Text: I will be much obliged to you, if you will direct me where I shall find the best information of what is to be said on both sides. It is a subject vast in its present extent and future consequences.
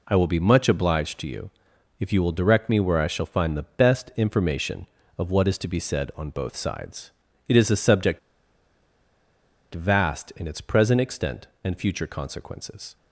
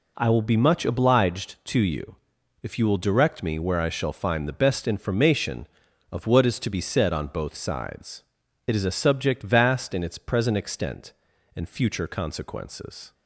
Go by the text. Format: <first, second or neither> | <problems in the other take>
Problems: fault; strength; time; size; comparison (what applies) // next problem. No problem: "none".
second | pauses between "subject" and "vast"; strong; at 8.1 s; 1.5 s long